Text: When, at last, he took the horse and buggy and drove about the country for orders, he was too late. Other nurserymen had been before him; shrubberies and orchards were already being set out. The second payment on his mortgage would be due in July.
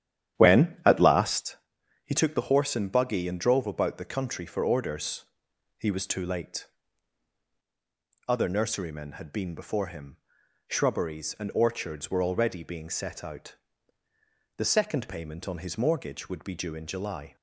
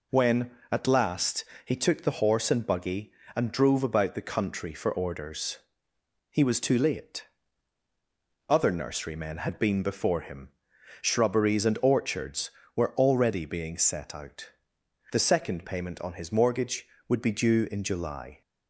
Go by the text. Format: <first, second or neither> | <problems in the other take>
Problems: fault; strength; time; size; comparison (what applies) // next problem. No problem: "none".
second | starts louder than the rest; strong; until 1.5 s; 11 dB